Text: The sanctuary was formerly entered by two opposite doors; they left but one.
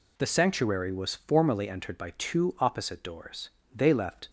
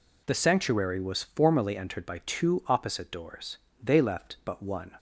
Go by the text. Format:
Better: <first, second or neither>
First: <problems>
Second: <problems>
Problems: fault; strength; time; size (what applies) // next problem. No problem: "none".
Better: second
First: stops before "but one"; at 4.2 s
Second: none